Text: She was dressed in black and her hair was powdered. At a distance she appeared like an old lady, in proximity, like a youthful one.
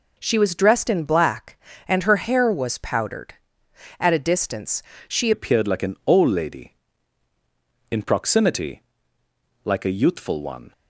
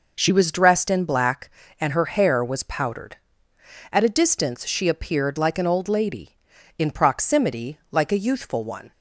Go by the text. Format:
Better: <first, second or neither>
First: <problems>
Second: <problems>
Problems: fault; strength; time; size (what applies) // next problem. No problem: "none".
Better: second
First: pauses between "distance" and "she"; slight; at 4.8 s; 0.24 s long // changes voice at "appeared"; from 5.3 s on; 5.4 s long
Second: none